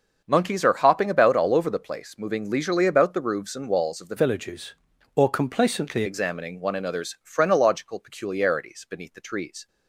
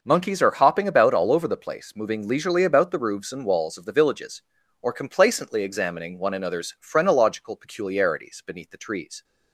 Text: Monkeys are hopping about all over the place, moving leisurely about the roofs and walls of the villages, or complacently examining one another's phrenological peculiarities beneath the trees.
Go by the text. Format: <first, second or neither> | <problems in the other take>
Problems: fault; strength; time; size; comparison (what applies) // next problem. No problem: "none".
second | starts louder than the rest; until 1.2 s; 6.5 dB // changes voice from "villages" to "complacently"; from 4.1 to 6.0 s; 1.9 s long